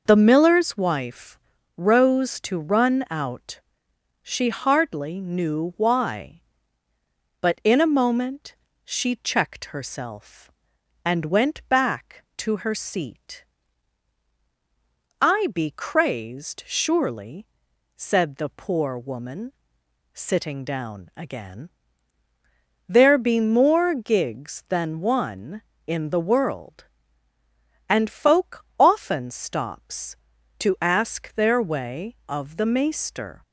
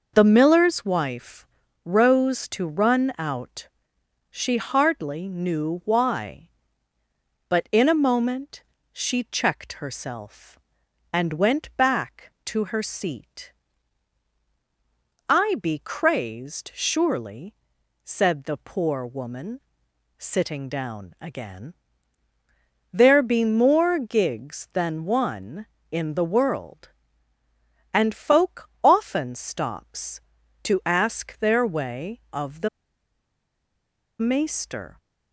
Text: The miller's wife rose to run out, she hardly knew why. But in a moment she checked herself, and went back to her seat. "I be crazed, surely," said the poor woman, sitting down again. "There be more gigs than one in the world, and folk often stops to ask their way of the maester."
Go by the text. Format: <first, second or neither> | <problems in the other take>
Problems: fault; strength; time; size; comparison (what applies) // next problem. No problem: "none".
first | pauses between "wife" and "rose"; at 1.4 s; 0.40 s long; also in the first // pauses between "moment" and "she"; slight; at 8.6 s; 0.30 s long; slight in the first // pauses between "the" and "maester"; strong; at 32.6 s; 1.5 s long